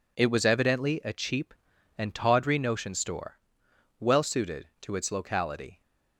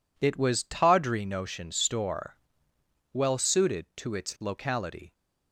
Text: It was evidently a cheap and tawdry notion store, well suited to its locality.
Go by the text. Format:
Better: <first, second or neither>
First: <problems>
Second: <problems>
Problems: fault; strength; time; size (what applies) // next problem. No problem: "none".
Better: first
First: none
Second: skips "evidently a cheap and"; at 0.6 s